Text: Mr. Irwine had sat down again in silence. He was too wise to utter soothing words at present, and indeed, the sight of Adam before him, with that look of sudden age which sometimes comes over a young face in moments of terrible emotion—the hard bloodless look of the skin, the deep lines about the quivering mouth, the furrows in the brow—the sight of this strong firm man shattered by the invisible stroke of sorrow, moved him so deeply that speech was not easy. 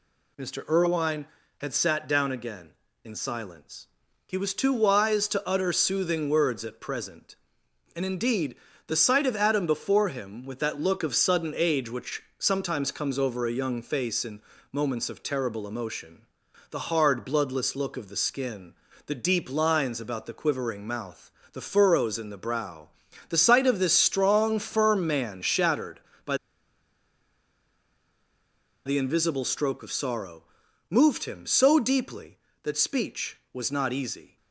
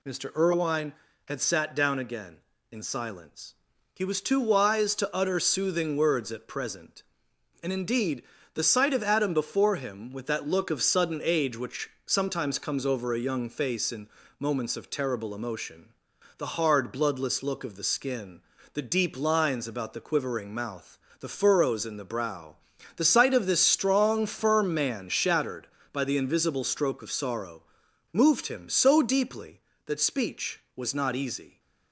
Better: second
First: pauses between "which" and "sometimes"; slight; at 12.2 s; 0.16 s long // pauses between "in" and "moments"; slight; at 14.4 s; 0.32 s long // pauses between "by" and "the"; strong; at 26.3 s; 2.4 s long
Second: pauses between "which" and "sometimes"; slight; at 11.8 s; 0.16 s long // pauses between "in" and "moments"; slight; at 14.0 s; 0.32 s long

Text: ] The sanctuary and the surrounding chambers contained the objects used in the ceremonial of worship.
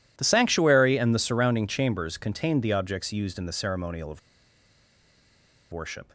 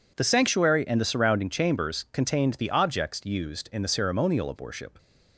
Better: second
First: pauses between "of" and "worship"; strong; at 4.1 s; 1.5 s long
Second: none

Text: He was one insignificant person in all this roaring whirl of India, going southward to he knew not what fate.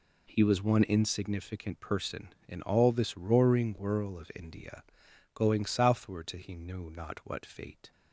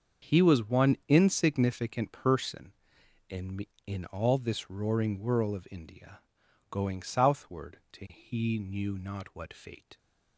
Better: first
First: none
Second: starts louder than the rest; until 1.3 s; 7 dB // says "in" twice; at 3.8 s

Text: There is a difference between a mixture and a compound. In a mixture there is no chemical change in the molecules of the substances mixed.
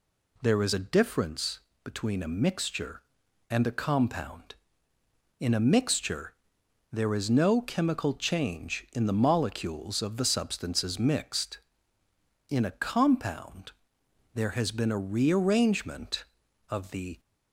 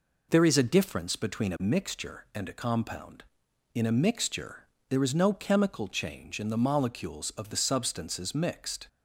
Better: second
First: pauses between "difference" and "between"; slight; at 1.5 s; 0.24 s long // pauses between "mixture" and "there"; noticeable; at 6.3 s; 0.58 s long // goes on to say "In a compound there has been a rearrangement of the"; strong; from 12.4 s on; 4.7 s long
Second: pauses between "mixture" and "there"; slight; at 4.5 s; 0.28 s long

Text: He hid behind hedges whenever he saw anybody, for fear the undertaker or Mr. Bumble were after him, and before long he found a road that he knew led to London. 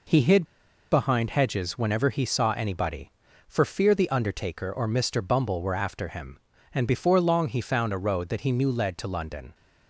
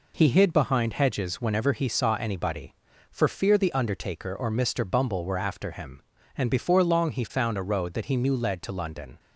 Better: second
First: pauses between "hid" and "behind"; at 0.4 s; 0.44 s long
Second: none

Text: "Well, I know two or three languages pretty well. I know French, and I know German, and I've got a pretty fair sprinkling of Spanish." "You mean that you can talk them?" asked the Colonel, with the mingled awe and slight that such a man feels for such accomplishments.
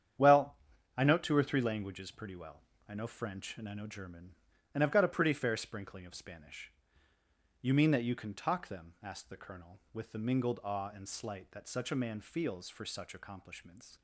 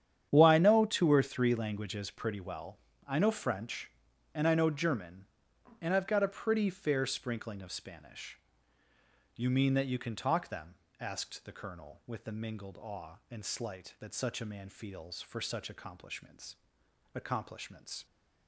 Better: first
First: starts louder than the rest; strong; until 1.5 s; 9 dB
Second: starts louder than the rest; strong; until 1.3 s; 9 dB // says "accomplishments" twice; at 17.1 s

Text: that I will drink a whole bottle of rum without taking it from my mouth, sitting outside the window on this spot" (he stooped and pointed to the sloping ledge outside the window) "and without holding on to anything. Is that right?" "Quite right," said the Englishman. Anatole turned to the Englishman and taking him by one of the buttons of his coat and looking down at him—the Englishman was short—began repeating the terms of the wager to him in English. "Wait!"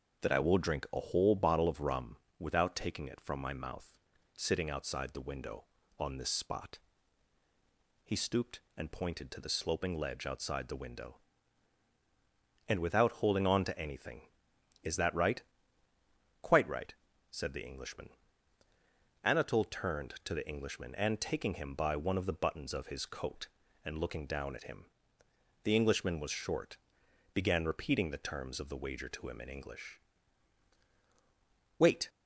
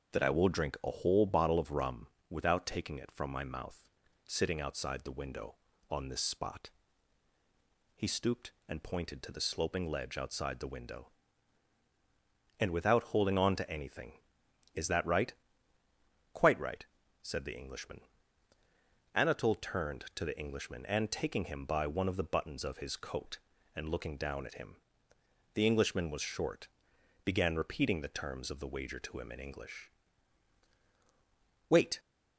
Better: neither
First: starts louder than the rest; until 1.2 s; 6.5 dB // pauses between "rum" and "without"; slight; at 2.1 s; 0.24 s long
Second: starts louder than the rest; until 1.1 s; 6.5 dB // pauses between "rum" and "without"; slight; at 2.0 s; 0.24 s long

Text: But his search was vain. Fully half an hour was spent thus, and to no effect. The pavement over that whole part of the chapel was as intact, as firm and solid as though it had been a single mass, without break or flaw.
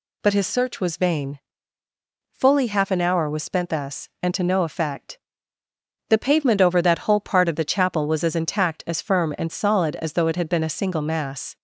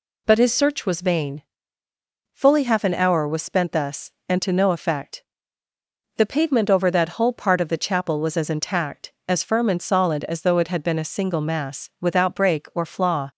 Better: second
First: stops before "without break or flaw"; at 11.5 s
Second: none

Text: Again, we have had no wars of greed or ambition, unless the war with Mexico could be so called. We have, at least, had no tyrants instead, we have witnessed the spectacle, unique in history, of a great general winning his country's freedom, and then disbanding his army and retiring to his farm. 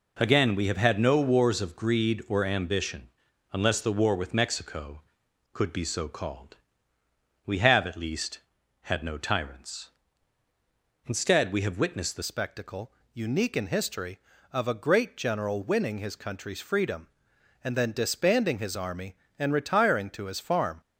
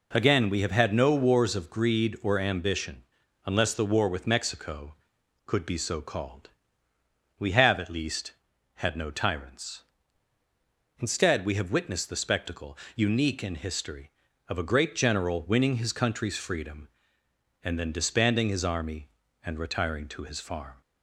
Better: second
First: changes voice at "spectacle"; from 12.2 s on; 8.6 s long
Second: none

